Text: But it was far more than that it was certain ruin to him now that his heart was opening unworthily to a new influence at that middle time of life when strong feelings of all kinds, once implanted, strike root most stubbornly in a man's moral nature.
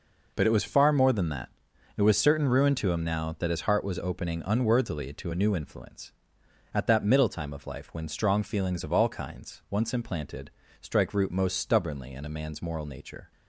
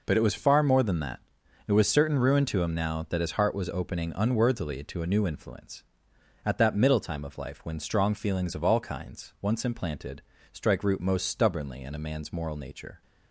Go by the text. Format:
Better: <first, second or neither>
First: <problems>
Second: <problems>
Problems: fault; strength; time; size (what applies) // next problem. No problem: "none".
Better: neither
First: pauses between "that" and "it"; noticeable; at 1.4 s; 0.46 s long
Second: pauses between "that" and "it"; noticeable; at 1.1 s; 0.46 s long